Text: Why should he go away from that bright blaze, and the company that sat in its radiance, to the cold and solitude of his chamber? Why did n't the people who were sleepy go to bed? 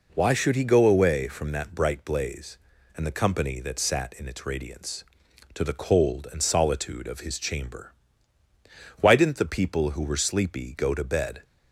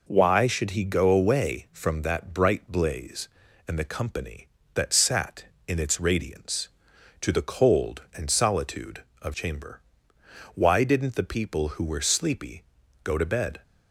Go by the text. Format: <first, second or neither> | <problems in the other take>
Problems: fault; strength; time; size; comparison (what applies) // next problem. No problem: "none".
first | skips "his"; at 9.3 s // pauses between "sleepy" and "go"; at 12.6 s; 0.40 s long